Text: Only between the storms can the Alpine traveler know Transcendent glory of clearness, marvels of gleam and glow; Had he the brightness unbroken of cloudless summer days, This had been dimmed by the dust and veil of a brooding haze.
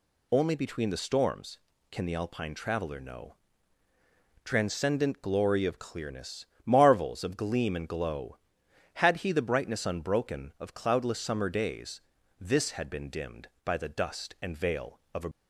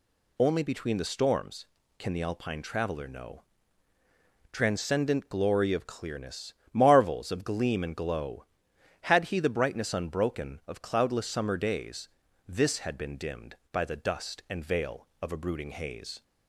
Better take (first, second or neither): second